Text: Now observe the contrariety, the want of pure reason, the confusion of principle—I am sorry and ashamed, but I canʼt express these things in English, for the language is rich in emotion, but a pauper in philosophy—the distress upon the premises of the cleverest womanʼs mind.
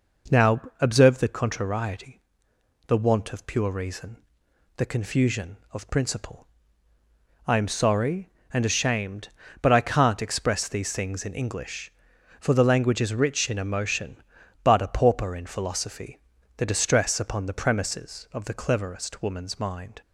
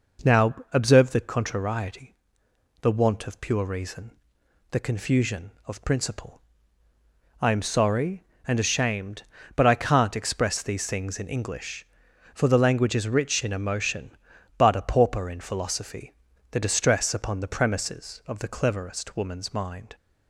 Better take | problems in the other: neither | pauses between "Now" and "observe"; slight; the same in both

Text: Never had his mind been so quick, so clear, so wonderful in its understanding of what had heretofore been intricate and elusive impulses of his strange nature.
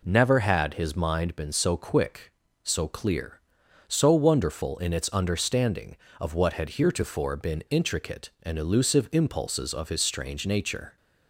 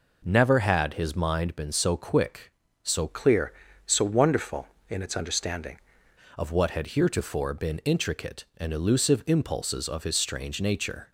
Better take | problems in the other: first | changes voice from "clear" to "understanding"; from 3.0 to 5.7 s; 2.7 s long

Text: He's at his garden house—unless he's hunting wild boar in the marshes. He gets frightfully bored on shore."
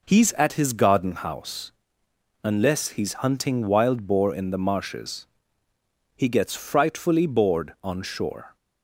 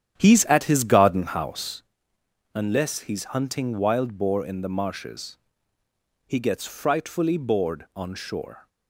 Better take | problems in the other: first | starts louder than the rest; strong; until 1.8 s; 10 dB

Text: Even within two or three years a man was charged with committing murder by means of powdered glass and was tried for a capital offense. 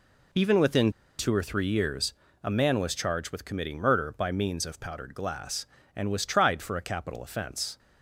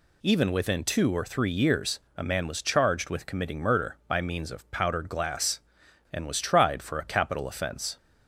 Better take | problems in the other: second | pauses between "within" and "two"; slight; at 0.8 s; 0.29 s long // pauses between "years" and "a"; slight; at 2.1 s; 0.28 s long; slight in the second

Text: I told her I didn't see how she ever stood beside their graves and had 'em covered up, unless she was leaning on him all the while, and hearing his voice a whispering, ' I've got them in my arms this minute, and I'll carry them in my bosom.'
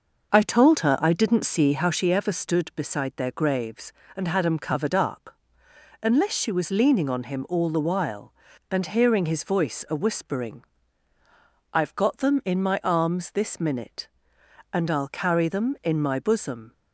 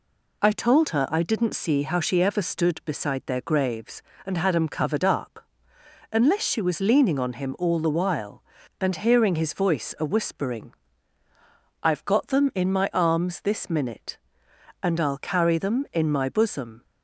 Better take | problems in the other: second | starts louder than the rest; noticeable; until 2.0 s; 6 dB

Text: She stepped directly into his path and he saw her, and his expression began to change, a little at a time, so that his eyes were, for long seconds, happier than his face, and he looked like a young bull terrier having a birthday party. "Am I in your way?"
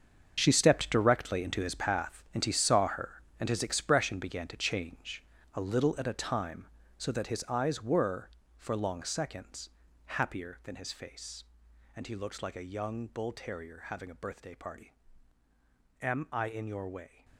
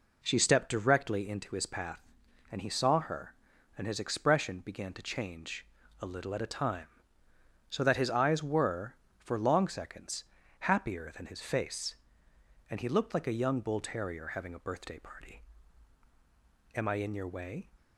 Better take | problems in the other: second | gets quieter; strong; throughout; 12.5 dB

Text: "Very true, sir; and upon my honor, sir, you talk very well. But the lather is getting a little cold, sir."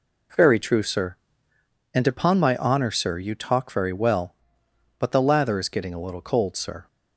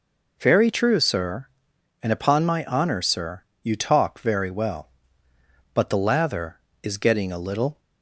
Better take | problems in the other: first | stops before "cold sir"; at 7.7 s

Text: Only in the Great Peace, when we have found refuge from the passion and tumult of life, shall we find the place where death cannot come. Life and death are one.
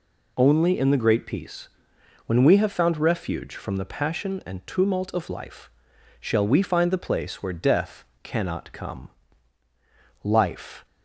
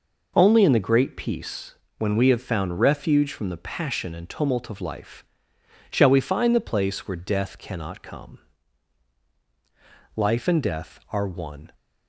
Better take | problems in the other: second | pauses between "death" and "cannot"; slight; at 8.0 s; 0.18 s long // stops before "and death are one"; at 10.8 s

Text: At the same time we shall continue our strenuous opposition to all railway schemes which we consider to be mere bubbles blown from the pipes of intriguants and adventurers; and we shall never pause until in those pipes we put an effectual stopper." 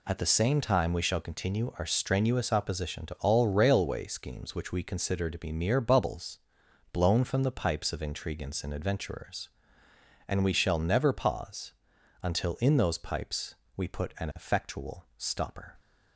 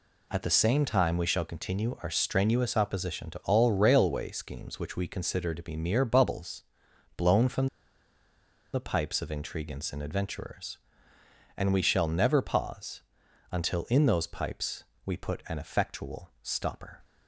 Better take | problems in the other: first | pauses between "bubbles" and "blown"; noticeable; at 6.6 s; 0.56 s long; noticeable in the first // pauses between "from" and "the"; at 7.6 s; 1.0 s long // pauses between "pause" and "until"; noticeable; at 13.0 s; 0.48 s long; noticeable in the first // pauses between "pipes" and "we"; slight; at 14.8 s; 0.20 s long; slight in the first

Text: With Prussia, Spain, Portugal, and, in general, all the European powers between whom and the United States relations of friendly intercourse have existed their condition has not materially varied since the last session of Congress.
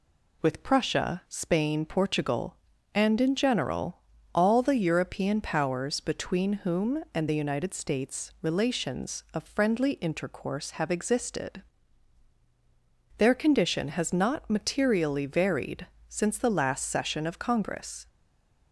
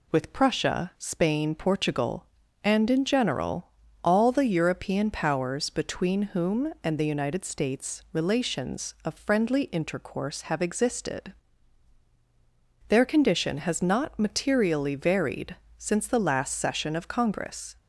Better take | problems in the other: second | pauses between "existed" and "their"; strong; at 11.6 s; 1.5 s long; strong in the second // pauses between "varied" and "since"; slight; at 15.8 s; 0.20 s long; slight in the second // stays silent after the last word; slight; from 18.0 s on; 0.7 s long

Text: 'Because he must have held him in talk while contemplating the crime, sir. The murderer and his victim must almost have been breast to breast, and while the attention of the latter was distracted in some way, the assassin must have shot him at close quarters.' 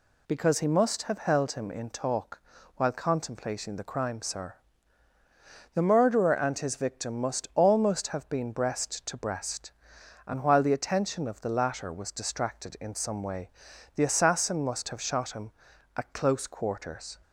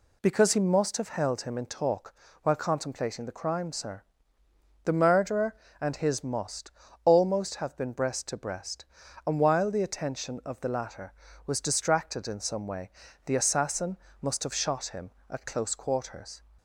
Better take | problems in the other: first | pauses between "talk" and "while"; slight; at 2.1 s; 0.30 s long; also in the first // skips "victim"; at 6.2 s // pauses between "must" and "almost"; slight; at 6.7 s; 0.34 s long // pauses between "assassin" and "must"; slight; at 13.9 s; 0.24 s long

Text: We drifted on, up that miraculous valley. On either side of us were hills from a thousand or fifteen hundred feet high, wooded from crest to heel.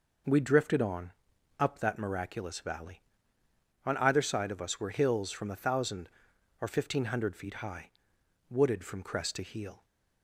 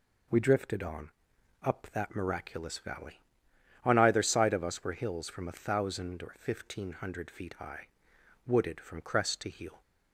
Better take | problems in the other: neither | none

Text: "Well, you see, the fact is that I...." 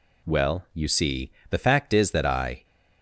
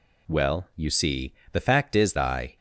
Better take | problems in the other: first | skips "that"; at 2.1 s

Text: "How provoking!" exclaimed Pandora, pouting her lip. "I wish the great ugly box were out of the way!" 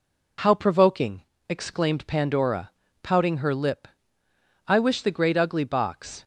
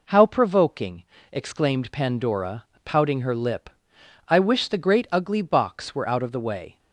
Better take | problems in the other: second | stops before "were out of the way"; at 6.2 s

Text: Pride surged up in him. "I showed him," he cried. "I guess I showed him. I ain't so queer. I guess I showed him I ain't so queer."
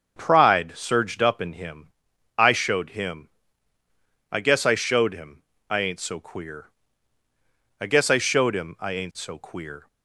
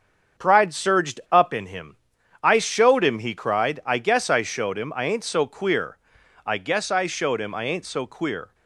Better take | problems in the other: second | starts louder than the rest; until 1.2 s; 7 dB; strong in the second // skips "he cried"; at 3.8 s

